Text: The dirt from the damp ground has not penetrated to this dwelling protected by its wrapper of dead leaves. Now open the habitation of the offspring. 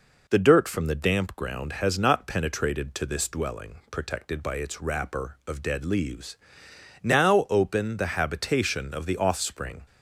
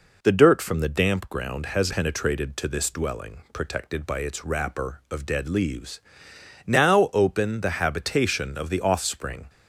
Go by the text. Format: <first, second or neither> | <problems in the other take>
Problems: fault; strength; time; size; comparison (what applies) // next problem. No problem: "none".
first | skips "not"; at 1.9 s